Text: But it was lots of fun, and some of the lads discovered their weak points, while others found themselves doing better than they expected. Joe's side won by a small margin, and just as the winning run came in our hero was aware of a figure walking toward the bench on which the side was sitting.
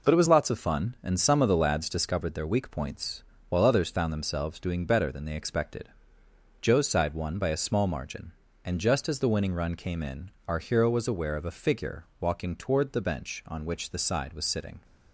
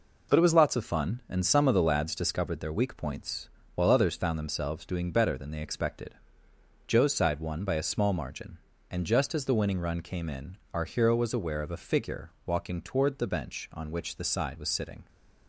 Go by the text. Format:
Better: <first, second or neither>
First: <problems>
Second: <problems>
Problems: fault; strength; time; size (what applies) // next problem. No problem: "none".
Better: neither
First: pauses between "in" and "our"; slight; at 10.2 s; 0.16 s long // pauses between "figure" and "walking"; slight; at 12.0 s; 0.16 s long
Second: pauses between "in" and "our"; slight; at 10.5 s; 0.15 s long // pauses between "figure" and "walking"; slight; at 12.2 s; 0.16 s long